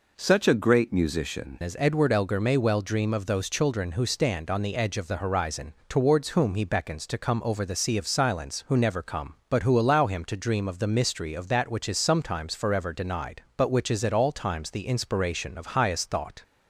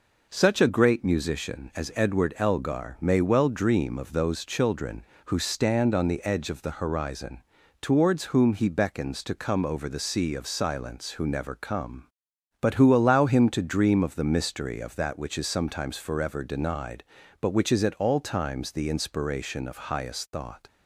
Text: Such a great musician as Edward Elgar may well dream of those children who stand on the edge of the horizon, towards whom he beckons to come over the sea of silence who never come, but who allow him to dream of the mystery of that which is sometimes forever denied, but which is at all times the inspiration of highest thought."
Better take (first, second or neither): second